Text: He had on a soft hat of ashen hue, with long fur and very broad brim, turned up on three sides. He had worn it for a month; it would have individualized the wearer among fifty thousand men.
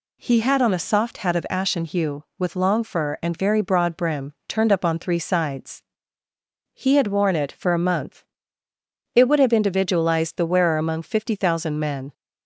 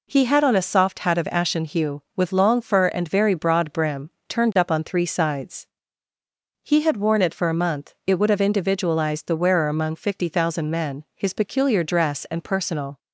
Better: first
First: none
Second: goes on to say "His peculiar dress and personal"; strong; from 11.1 s on; 1.8 s long

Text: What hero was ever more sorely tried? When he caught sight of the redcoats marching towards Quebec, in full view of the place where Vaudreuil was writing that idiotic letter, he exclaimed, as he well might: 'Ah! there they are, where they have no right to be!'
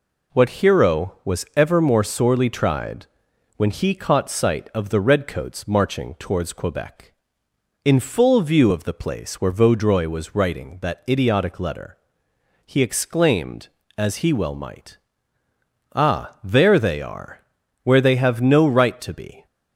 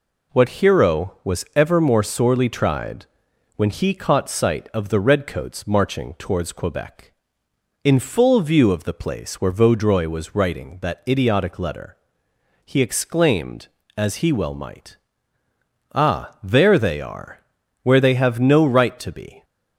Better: neither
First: none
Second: none

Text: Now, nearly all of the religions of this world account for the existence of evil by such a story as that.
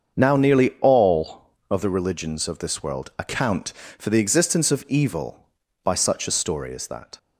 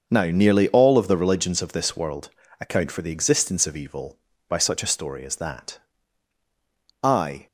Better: first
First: starts louder than the rest; until 1.2 s; 7 dB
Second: starts louder than the rest; noticeable; until 1.0 s; 6 dB // pauses between "world" and "account"; slight; at 2.3 s; 0.30 s long // goes on to say "I"; slight; from 7.0 s on; 0.44 s long

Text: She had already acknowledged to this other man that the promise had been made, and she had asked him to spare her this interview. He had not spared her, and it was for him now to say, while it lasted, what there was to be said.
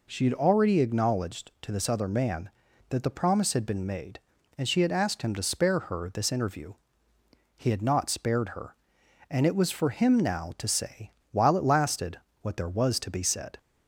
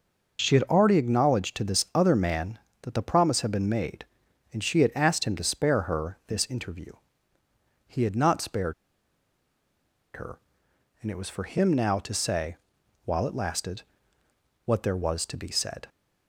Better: first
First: none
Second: pauses between "spared" and "her"; strong; at 8.7 s; 1.4 s long

